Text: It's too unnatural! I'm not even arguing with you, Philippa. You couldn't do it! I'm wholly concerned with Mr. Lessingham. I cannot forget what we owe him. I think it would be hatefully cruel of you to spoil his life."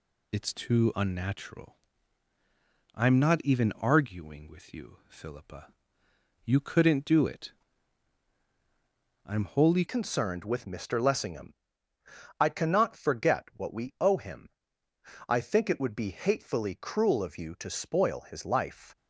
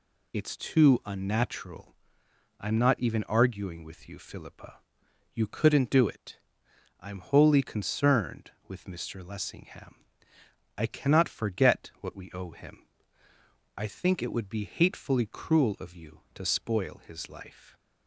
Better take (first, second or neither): second